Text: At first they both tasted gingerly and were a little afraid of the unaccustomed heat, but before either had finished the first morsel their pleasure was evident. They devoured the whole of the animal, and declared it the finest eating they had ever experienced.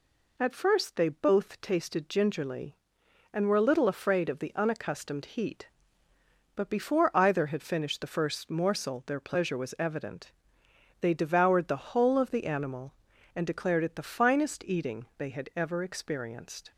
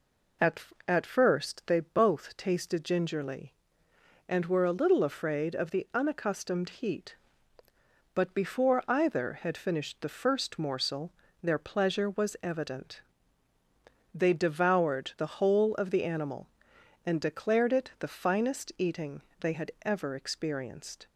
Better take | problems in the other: first | says "At" twice; at 0.8 s // pauses between "morsel" and "their"; slight; at 11.1 s; 0.30 s long // pauses between "eating" and "they"; slight; at 19.2 s; 0.18 s long

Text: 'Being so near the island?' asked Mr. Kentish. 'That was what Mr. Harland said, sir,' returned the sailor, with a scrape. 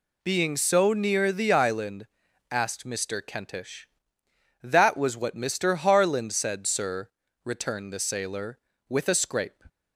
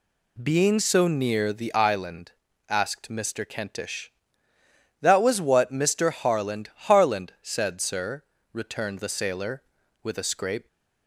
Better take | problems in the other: first | says "Harland" twice; at 6.7 s

